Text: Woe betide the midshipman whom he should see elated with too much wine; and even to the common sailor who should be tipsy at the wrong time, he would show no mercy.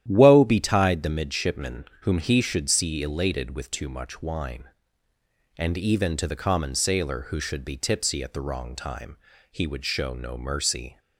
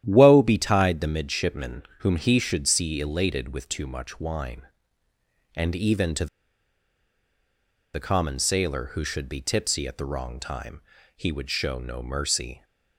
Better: first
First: starts louder than the rest; strong; until 1.0 s; 11 dB // pauses between "midshipman" and "whom"; slight; at 1.8 s; 0.20 s long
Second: starts louder than the rest; strong; until 1.0 s; 11 dB // pauses between "midshipman" and "whom"; slight; at 1.8 s; 0.20 s long // pauses between "to" and "the"; strong; at 6.2 s; 1.6 s long

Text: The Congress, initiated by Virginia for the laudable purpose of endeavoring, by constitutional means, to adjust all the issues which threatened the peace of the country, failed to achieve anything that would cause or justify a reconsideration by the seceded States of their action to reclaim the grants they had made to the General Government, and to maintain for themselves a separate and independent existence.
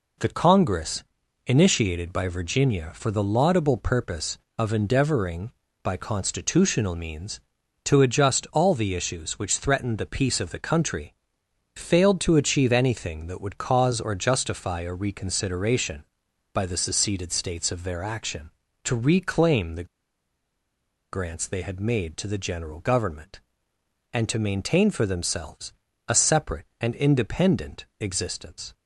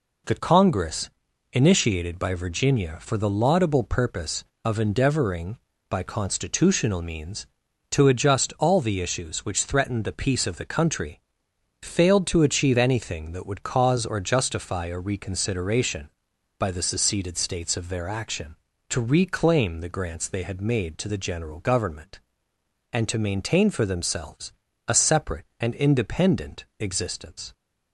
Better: second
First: pauses between "the" and "grants"; strong; at 19.8 s; 1.2 s long // pauses between "themselves" and "a"; slight; at 25.7 s; 0.34 s long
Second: pauses between "themselves" and "a"; slight; at 24.5 s; 0.34 s long

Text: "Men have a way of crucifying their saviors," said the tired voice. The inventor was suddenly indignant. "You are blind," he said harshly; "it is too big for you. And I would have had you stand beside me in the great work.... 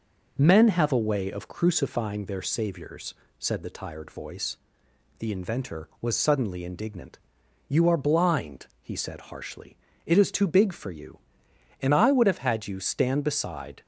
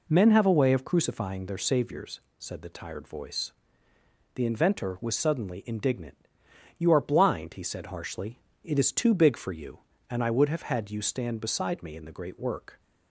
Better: second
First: stops before "me in the great work"; at 13.8 s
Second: none

